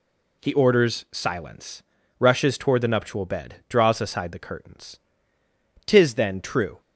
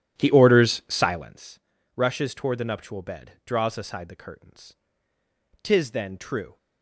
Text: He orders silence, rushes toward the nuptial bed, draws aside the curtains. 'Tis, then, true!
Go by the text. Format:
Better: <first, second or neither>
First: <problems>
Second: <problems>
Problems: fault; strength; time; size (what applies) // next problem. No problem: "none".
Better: first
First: none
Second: starts louder than the rest; strong; until 1.3 s; 11 dB